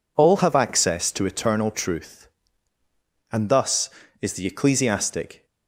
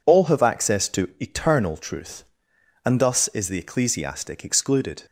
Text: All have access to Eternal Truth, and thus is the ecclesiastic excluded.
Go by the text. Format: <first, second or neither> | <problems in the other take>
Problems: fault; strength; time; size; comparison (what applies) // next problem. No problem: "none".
second | stops before "excluded"; at 5.4 s